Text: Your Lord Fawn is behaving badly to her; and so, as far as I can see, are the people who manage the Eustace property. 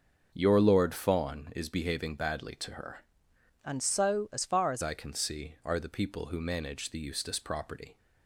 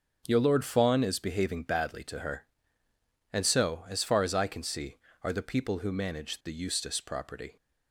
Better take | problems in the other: second | starts louder than the rest; until 1.3 s; 6.5 dB; also in the second // changes voice from "and" to "as"; from 3.6 to 4.8 s; 1.2 s long

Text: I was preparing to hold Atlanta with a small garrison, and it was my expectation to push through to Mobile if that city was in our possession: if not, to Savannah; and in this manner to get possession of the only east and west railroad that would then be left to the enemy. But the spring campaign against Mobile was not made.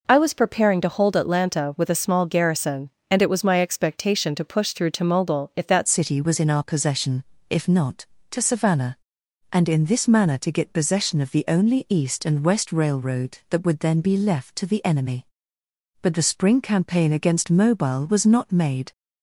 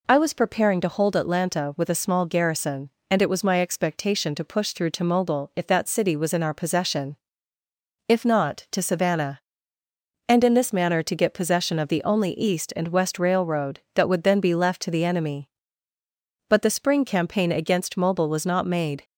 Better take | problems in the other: second | changes voice at "city"; from 5.8 s on; 13.1 s long

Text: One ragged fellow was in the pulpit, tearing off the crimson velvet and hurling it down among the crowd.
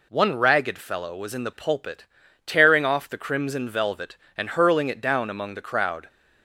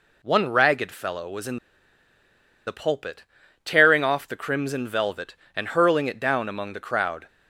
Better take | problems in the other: first | pauses between "in" and "the"; at 1.5 s; 1.0 s long

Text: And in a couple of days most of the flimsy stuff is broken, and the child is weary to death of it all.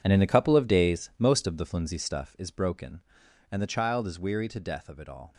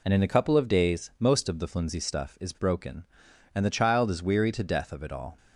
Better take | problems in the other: second | gets quieter; strong; throughout; 13.5 dB

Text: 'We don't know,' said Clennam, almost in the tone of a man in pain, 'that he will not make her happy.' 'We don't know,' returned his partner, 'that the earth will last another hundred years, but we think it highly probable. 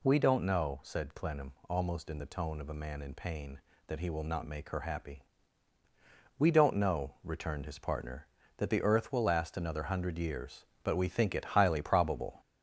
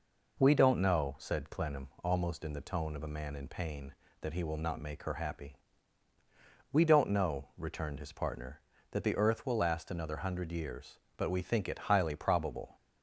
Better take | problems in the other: second | gets louder; throughout; 4 dB

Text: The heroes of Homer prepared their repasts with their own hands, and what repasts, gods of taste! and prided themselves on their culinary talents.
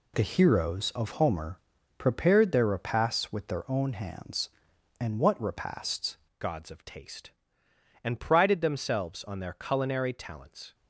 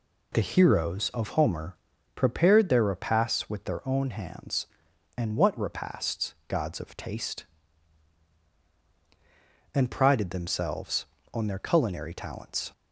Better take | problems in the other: second | pauses between "Homer" and "prepared"; at 1.5 s; 0.40 s long; also in the second // changes voice at "gods"; from 6.3 s on; 4.4 s long

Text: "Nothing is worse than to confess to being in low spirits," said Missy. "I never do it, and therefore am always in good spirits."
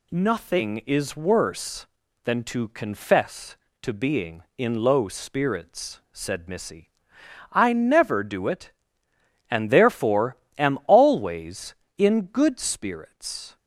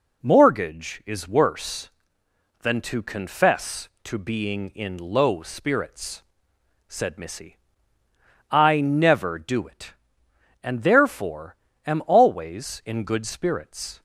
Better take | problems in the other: first | says "Mortgage" for "Nothing"; at 0.2 s // pauses between "therefore" and "am"; slight; at 11.5 s; 0.30 s long; slight in the first

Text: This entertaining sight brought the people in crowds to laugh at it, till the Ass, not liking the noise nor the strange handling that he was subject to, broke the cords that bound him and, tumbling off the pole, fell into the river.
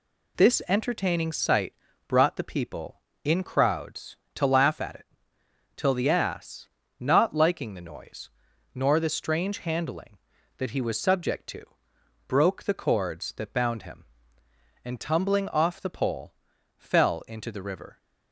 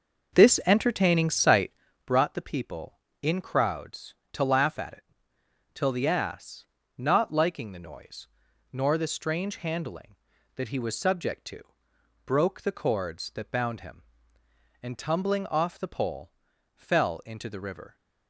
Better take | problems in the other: first | starts louder than the rest; noticeable; until 1.8 s; 6 dB // pauses between "sight" and "brought"; slight; at 1.6 s; 0.36 s long; slight in the first // pauses between "noise" and "nor"; noticeable; at 8.2 s; 0.46 s long; noticeable in the first

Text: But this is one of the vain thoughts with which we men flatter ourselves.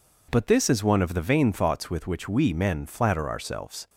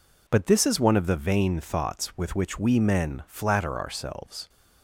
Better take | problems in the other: neither | none

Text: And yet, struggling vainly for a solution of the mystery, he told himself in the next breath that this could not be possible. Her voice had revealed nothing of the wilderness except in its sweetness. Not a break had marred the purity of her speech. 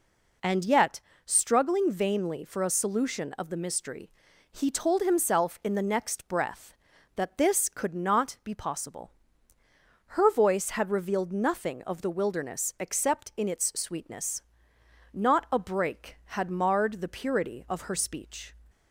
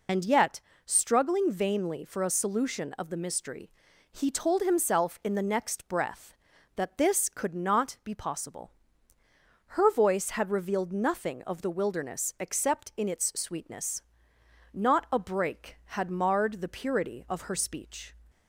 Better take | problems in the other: first | loses the start of "And"; at 0.0 s; 75 ms

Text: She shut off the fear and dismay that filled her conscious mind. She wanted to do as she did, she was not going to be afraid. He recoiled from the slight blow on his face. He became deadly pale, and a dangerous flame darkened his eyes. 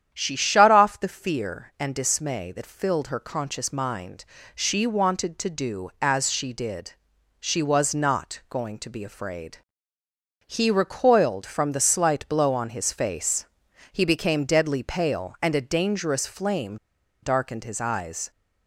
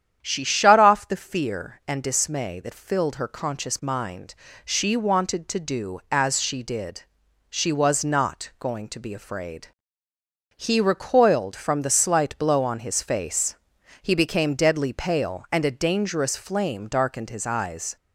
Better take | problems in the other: second | starts louder than the rest; strong; until 1.1 s; 9.5 dB; strong in the second // pauses between "flame" and "darkened"; noticeable; at 16.7 s; 0.46 s long

